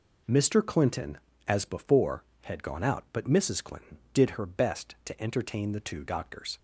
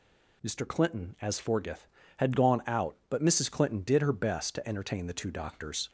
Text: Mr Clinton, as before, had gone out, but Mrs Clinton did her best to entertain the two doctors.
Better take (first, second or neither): first